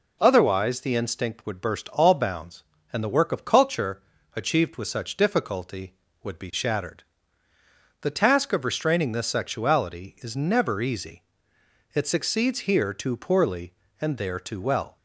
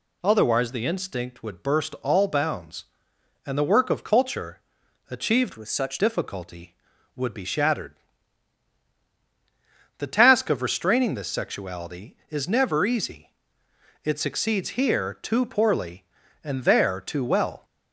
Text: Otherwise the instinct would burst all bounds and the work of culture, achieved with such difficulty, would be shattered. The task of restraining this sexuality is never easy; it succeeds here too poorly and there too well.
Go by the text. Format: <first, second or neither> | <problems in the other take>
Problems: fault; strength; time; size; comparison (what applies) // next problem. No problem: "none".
first | changes voice from "with" to "such"; from 5.5 to 5.9 s; 0.4 s long